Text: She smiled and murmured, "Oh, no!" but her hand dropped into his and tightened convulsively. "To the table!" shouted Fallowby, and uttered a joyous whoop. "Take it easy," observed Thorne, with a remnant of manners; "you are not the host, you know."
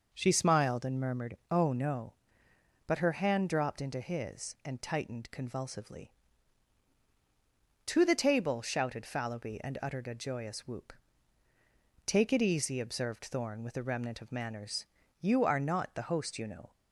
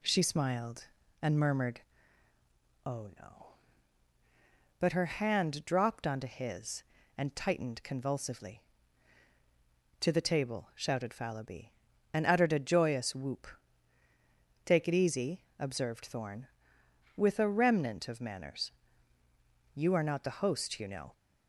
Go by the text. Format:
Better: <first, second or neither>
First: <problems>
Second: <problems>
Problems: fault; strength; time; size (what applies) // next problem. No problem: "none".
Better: first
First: none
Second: says "onto" for "into"; at 6.0 s